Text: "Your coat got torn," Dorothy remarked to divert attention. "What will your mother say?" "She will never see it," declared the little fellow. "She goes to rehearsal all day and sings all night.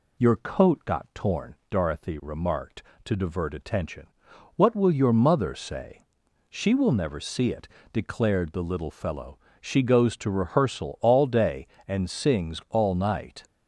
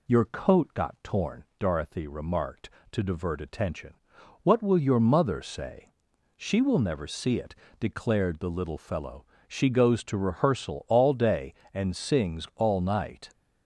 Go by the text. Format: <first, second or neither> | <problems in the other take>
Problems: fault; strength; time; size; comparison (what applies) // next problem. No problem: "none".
neither | none